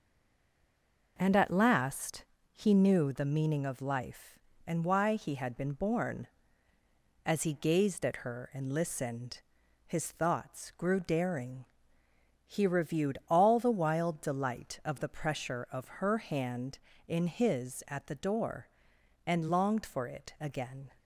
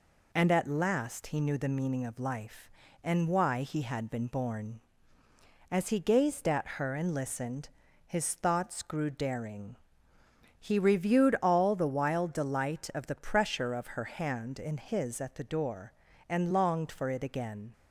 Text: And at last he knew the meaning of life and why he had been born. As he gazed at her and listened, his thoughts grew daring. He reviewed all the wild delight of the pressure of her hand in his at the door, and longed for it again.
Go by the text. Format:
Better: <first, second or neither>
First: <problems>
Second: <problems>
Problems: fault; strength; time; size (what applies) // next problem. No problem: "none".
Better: second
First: stays silent before the first word; until 1.1 s; 1.1 s long // pauses between "last" and "he"; slight; at 2.2 s; 0.30 s long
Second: none